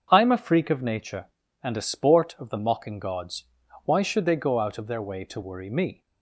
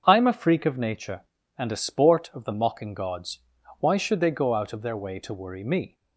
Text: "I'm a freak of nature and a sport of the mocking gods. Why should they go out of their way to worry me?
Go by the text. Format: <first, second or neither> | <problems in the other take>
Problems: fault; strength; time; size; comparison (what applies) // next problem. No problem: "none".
neither | starts louder than the rest; the same in both